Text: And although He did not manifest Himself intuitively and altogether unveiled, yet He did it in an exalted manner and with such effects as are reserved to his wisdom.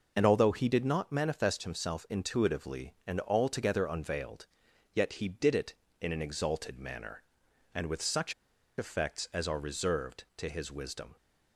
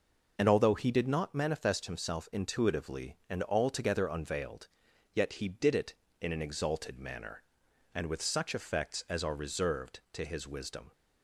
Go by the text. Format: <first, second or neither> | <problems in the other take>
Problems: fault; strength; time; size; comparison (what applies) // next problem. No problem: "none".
second | pauses between "such" and "effects"; noticeable; at 8.3 s; 0.46 s long